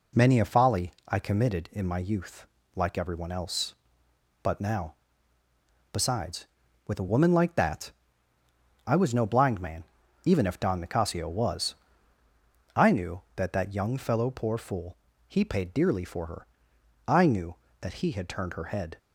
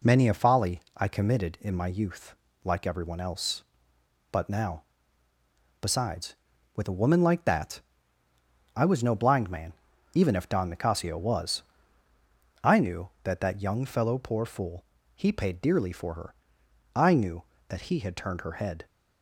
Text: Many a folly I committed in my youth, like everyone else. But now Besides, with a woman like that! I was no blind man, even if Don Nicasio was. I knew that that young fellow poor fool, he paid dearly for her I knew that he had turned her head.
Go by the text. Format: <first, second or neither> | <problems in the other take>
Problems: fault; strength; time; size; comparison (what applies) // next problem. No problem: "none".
neither | pauses between "folly" and "I"; slight; the same in both // pauses between "now" and "Besides"; noticeable; the same in both // pauses between "her" and "I"; noticeable; the same in both